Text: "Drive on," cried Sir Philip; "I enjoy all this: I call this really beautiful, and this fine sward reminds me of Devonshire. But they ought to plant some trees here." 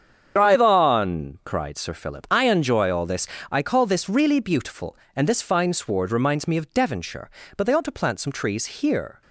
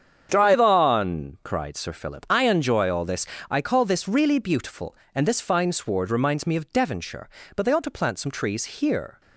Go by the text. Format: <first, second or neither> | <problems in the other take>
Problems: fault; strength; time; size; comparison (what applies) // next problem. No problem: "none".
second | loses the start of "Drive"; at 0.3 s; 55 ms // starts louder than the rest; strong; until 1.3 s; 8 dB; strong in the second